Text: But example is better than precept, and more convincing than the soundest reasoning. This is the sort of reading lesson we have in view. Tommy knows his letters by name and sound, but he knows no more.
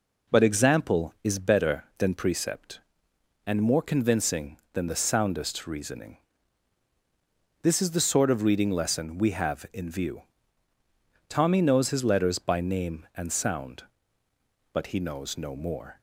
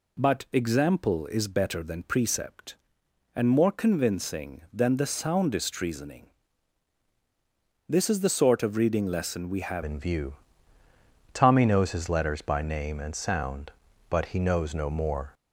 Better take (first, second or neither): first